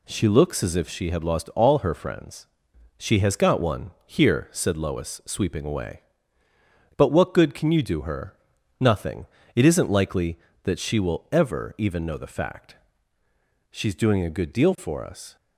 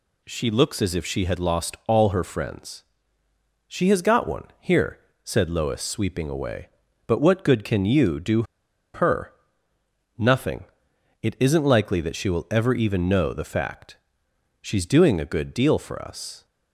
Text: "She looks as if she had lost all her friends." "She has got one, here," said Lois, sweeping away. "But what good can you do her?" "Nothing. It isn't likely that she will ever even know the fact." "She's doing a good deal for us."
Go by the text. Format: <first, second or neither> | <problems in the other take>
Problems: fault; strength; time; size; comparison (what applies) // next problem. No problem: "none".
first | pauses between "do" and "her"; noticeable; at 8.4 s; 0.51 s long